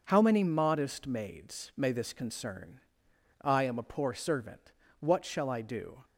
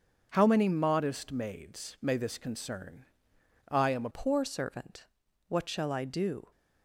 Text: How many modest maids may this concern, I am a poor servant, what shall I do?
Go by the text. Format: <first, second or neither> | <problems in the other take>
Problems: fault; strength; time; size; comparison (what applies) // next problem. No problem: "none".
first | starts louder than the rest; until 1.3 s; 6.5 dB; noticeable in the first // changes voice at "poor"; from 4.1 s on; 2.3 s long